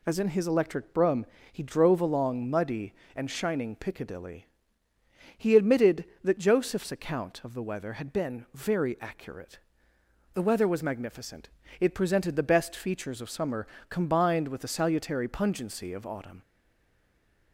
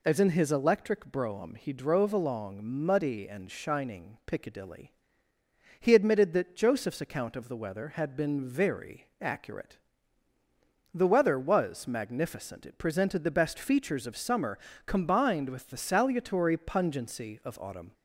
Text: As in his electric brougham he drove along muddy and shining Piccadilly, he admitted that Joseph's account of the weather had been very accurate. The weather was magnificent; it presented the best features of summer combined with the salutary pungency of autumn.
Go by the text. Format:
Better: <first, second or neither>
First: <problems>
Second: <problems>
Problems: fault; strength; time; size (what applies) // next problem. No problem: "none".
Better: second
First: pauses between "brougham" and "he"; slight; at 1.2 s; 0.28 s long // pauses between "summer" and "combined"; slight; at 13.6 s; 0.24 s long // stays silent after the last word; from 16.4 s on; 1.1 s long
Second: pauses between "summer" and "combined"; slight; at 14.5 s; 0.26 s long